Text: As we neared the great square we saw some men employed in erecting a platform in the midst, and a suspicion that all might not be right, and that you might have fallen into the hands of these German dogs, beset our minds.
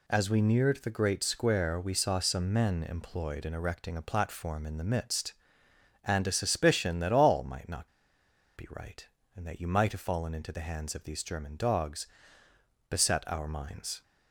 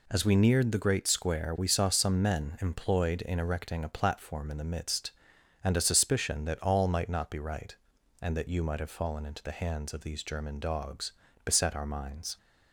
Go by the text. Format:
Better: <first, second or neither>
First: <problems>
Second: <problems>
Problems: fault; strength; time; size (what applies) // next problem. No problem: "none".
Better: second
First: pauses between "not" and "be"; noticeable; at 7.8 s; 0.68 s long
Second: none